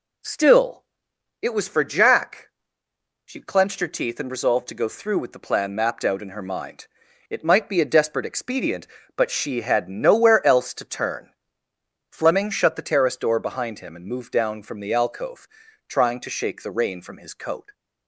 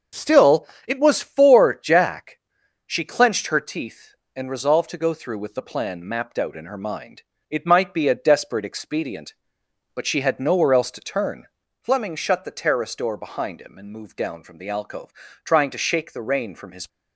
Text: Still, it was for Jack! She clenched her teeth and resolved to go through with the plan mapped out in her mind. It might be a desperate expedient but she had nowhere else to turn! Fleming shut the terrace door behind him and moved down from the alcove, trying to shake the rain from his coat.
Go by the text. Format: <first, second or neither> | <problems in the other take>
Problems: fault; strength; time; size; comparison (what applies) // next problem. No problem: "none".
first | starts louder than the rest; until 1.3 s; 6.5 dB // stops before "coat"; at 16.8 s